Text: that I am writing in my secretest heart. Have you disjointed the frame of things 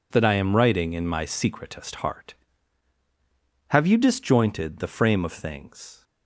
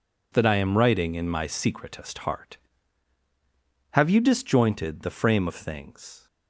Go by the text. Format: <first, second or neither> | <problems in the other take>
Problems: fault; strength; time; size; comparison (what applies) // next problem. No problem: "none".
neither | none